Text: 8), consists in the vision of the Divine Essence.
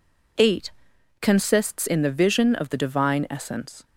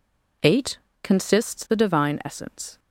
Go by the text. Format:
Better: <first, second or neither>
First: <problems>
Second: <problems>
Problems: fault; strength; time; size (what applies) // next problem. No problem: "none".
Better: first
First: none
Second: skips "in the vision of"; at 1.6 s